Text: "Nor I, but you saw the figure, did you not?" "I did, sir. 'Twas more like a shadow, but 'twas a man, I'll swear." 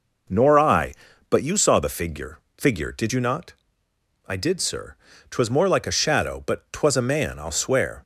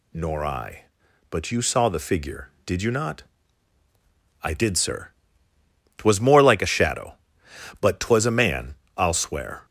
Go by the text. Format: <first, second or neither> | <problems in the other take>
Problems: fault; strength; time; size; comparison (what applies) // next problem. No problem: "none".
second | says "figure" twice; at 2.5 s